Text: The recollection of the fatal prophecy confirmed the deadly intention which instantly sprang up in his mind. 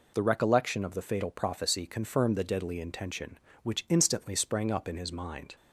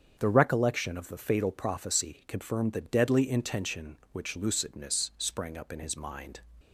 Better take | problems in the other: first | starts louder than the rest; strong; until 1.2 s; 7.5 dB // says "lucidness" for "instantly"; at 4.3 s

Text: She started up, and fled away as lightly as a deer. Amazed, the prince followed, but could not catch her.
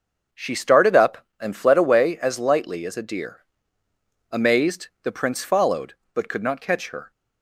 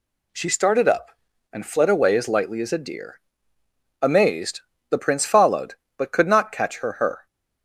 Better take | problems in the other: first | says "her" twice; at 6.9 s

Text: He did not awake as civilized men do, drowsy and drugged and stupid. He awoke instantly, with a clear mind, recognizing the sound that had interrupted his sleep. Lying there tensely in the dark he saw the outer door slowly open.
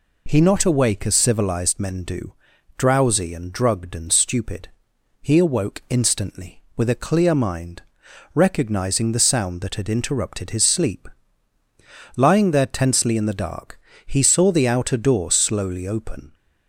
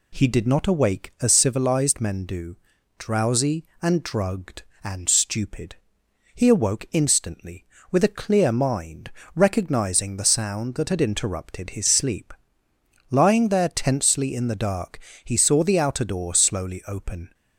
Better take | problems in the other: second | skips "did"; at 0.4 s // pauses between "dark" and "he"; slight; at 13.7 s; 0.26 s long; slight in the second

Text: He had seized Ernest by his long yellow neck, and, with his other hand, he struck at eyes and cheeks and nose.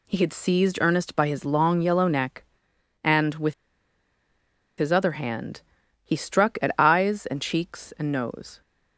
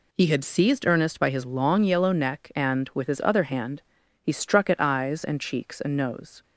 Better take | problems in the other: second | pauses between "with" and "his"; strong; at 3.5 s; 1.2 s long

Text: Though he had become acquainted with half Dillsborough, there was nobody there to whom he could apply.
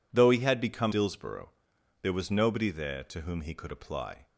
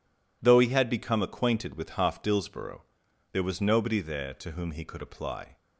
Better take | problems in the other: second | skips "acquainted with half"; at 0.9 s

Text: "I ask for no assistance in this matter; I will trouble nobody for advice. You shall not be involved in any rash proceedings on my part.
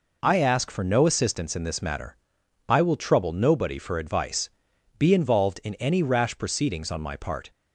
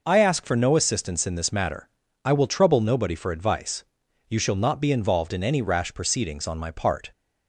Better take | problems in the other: second | skips "You shall not"; at 4.7 s

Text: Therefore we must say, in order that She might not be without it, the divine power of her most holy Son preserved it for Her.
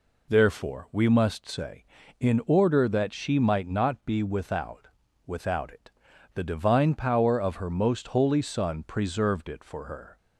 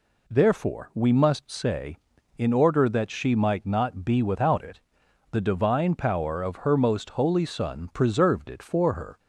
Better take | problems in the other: second | says "without" twice; at 5.2 s

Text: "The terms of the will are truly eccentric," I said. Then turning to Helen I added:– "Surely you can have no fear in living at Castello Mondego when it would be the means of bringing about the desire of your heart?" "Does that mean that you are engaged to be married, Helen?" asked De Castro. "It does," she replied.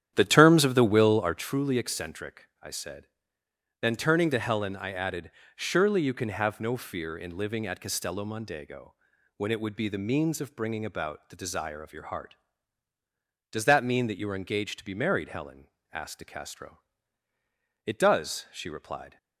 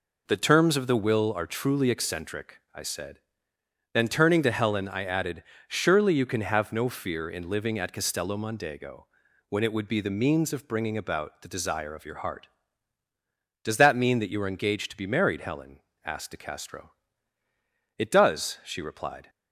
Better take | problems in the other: second | starts louder than the rest; strong; until 1.4 s; 10 dB // pauses between "Mondego" and "when"; at 8.9 s; 0.44 s long; also in the second

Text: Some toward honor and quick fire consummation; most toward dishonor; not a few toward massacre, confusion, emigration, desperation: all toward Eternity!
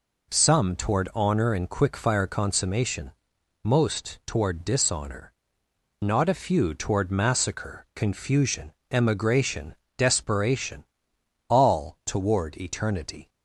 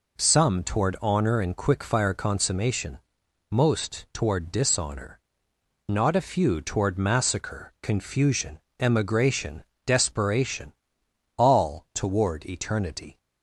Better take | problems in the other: neither | none

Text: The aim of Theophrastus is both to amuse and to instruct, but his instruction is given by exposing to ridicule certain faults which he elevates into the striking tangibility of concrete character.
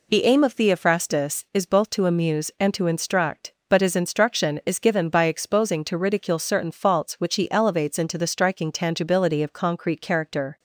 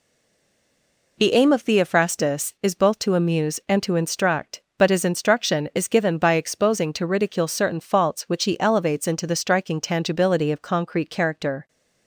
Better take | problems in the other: first | stays silent before the first word; noticeable; until 1.1 s; 1.1 s long

